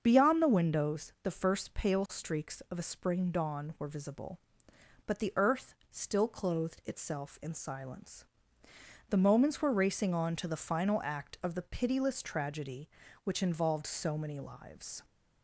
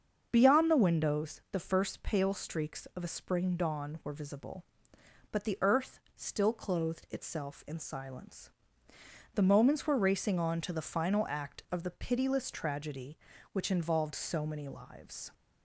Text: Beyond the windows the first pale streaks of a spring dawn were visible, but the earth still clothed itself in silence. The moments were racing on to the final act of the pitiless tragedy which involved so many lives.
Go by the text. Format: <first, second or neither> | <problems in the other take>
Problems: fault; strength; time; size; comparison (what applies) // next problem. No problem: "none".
neither | starts louder than the rest; the same in both // pauses between "earth" and "still"; slight; the same in both